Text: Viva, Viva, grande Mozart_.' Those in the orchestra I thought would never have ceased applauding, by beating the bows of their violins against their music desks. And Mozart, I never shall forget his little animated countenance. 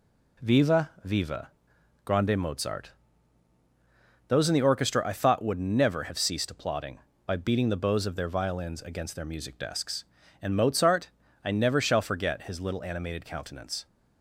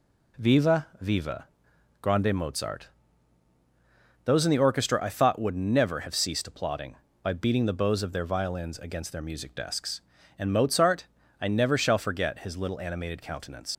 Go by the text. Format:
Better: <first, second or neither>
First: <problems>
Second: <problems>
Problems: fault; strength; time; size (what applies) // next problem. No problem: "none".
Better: first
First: none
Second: leaves "countenance" unfinished; at 13.7 s; 80 ms